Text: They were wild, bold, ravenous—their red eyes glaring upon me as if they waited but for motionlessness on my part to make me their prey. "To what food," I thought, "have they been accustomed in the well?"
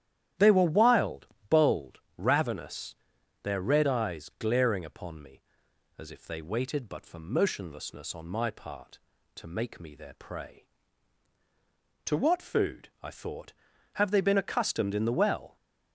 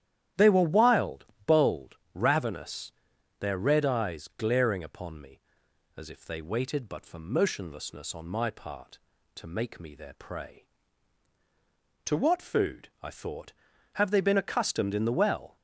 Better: neither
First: starts louder than the rest; strong; until 1.6 s; 11.5 dB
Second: starts louder than the rest; strong; until 1.5 s; 11.5 dB

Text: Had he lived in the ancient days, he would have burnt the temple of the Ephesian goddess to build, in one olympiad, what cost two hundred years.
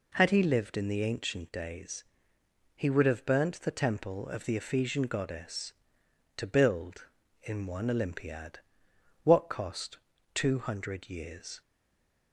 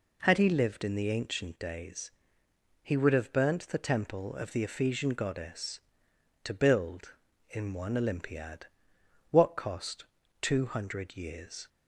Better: second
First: pauses between "cost" and "two"; slight; at 9.9 s; 0.36 s long // stays silent after the last word; slight; from 11.6 s on; 0.7 s long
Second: pauses between "cost" and "two"; slight; at 10.0 s; 0.36 s long

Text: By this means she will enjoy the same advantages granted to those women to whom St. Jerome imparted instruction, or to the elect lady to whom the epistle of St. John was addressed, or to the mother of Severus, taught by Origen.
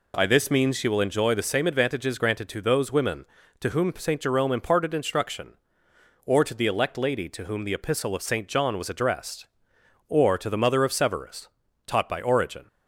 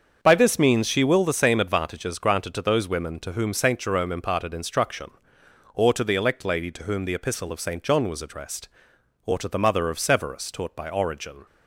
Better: first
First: none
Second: starts louder than the rest; until 1.2 s; 7 dB // skips "enjoy"; at 1.2 s

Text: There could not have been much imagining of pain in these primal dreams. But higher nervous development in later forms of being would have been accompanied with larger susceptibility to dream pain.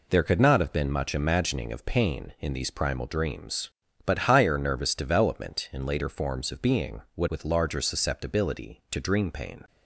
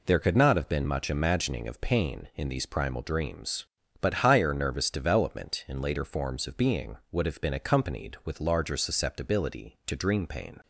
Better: second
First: skips "have been accompanied"; at 7.2 s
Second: none

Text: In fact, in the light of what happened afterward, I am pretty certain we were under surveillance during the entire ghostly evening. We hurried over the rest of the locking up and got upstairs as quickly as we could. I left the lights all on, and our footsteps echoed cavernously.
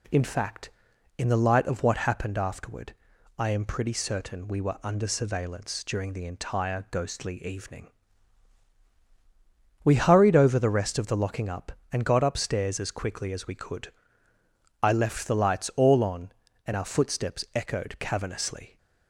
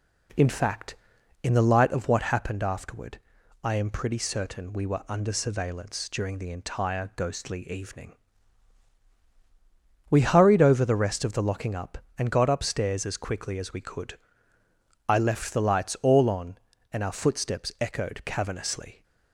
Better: first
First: none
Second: starts louder than the rest; slight; until 2.0 s; 3 dB

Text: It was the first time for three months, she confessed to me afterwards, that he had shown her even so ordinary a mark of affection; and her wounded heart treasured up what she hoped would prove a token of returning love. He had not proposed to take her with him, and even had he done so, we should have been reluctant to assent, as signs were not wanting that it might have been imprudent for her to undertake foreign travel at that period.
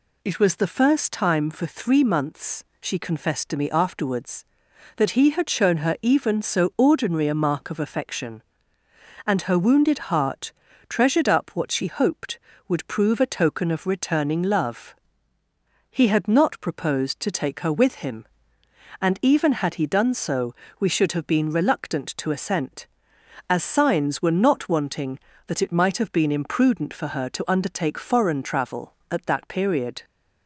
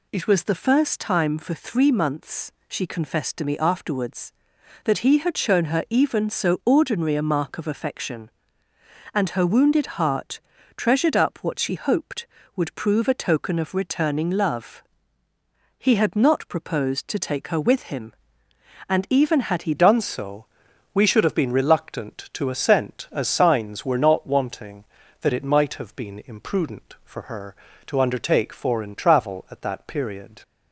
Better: first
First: pauses between "heart" and "treasured"; at 10.5 s; 0.38 s long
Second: pauses between "heart" and "treasured"; at 10.3 s; 0.38 s long // changes voice at "done"; from 19.7 s on; 10.7 s long

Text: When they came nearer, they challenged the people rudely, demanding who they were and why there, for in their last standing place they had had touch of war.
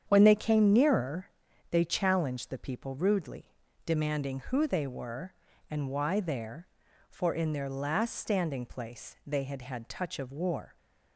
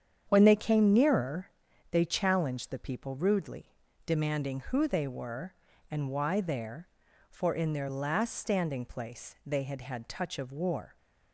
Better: neither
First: starts louder than the rest; strong; until 1.0 s; 8 dB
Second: starts louder than the rest; strong; until 1.3 s; 8 dB

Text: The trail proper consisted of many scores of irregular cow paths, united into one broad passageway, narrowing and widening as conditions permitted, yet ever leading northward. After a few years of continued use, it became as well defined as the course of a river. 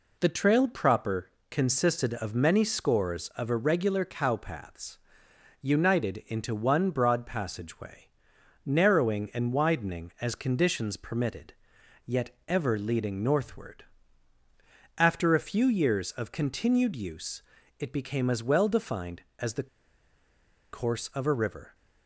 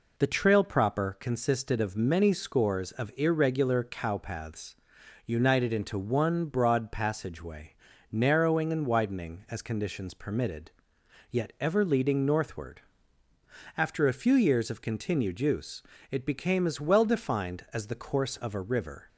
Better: second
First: pauses between "proper" and "consisted"; slight; at 1.2 s; 0.22 s long // pauses between "yet" and "ever"; slight; at 12.3 s; 0.16 s long // pauses between "the" and "course"; at 19.6 s; 1.0 s long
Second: none

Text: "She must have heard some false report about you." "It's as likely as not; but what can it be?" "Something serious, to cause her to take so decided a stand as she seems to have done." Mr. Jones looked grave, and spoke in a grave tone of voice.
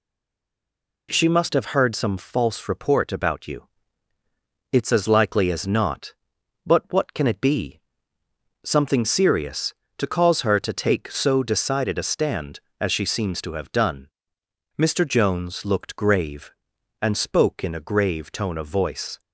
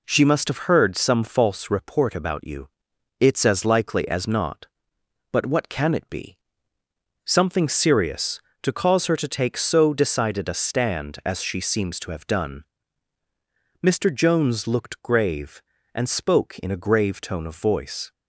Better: second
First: stays silent before the first word; until 1.0 s; 1.0 s long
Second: none

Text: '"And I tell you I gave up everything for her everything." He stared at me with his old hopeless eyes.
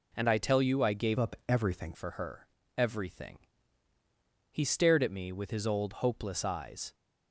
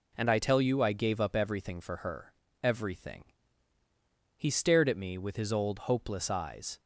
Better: second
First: changes voice from "up" to "everything"; from 1.1 to 1.9 s; 0.8 s long // pauses between "her" and "everything"; slight; at 2.4 s; 0.30 s long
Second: pauses between "her" and "everything"; slight; at 2.3 s; 0.30 s long

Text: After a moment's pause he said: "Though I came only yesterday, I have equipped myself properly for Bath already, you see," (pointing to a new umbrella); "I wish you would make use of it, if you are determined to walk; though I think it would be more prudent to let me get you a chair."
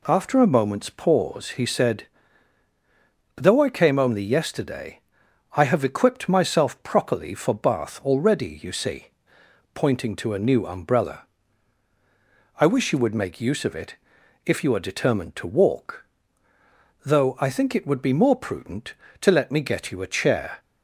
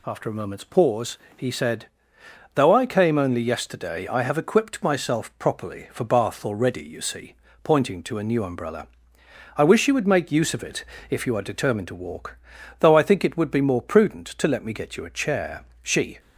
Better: first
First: none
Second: pauses between "pause" and "he"; slight; at 1.1 s; 0.18 s long // goes on to say "She"; slight; from 15.8 s on; 0.38 s long

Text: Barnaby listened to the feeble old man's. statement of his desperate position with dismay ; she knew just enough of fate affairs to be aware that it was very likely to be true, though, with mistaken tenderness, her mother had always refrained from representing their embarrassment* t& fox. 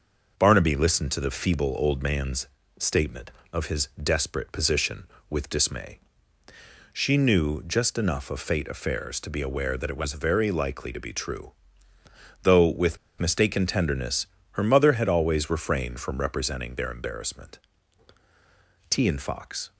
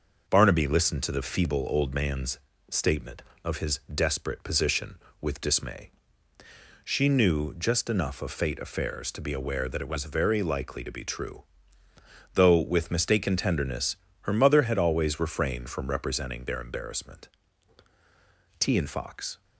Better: second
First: starts louder than the rest; noticeable; until 1.3 s; 6 dB // pauses between "with" and "mistaken"; slight; at 12.9 s; 0.22 s long // pauses between "embarrassment" and "t"; strong; at 17.5 s; 1.3 s long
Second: starts louder than the rest; noticeable; until 1.2 s; 6 dB // pauses between "embarrassment" and "t"; strong; at 17.2 s; 1.3 s long

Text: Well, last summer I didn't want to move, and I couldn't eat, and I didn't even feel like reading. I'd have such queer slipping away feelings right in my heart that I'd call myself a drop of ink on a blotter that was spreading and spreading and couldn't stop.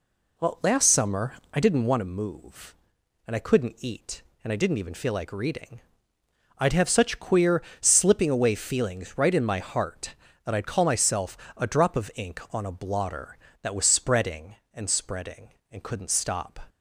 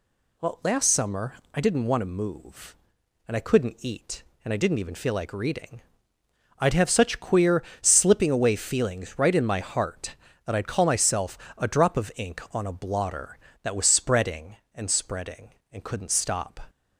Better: second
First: starts louder than the rest; slight; until 2.0 s; 3 dB // pauses between "summer" and "I"; slight; at 1.3 s; 0.22 s long // pauses between "queer" and "slipping"; slight; at 7.6 s; 0.18 s long // pauses between "myself" and "a"; slight; at 11.3 s; 0.18 s long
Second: pauses between "summer" and "I"; slight; at 1.3 s; 0.22 s long // pauses between "queer" and "slipping"; slight; at 7.6 s; 0.18 s long // pauses between "myself" and "a"; slight; at 11.3 s; 0.18 s long

